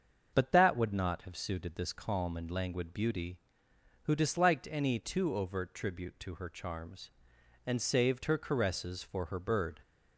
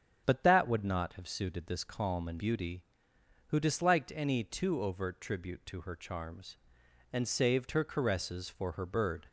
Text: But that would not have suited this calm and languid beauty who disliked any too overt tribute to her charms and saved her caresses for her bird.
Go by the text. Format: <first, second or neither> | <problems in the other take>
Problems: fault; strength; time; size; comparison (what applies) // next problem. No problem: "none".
first | starts louder than the rest; strong; until 1.2 s; 8 dB; also in the first // skips "languid"; at 2.3 s